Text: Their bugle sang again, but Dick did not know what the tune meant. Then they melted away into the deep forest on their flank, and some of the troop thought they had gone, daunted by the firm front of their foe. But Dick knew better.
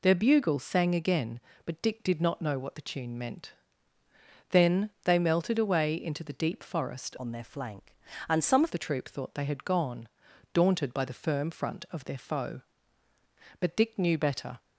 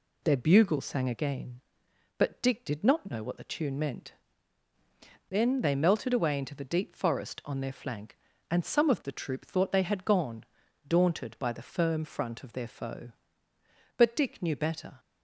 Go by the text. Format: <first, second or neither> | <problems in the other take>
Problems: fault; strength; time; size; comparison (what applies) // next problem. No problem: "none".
second | changes voice from "on" to "of"; from 7.1 to 8.7 s; 1.6 s long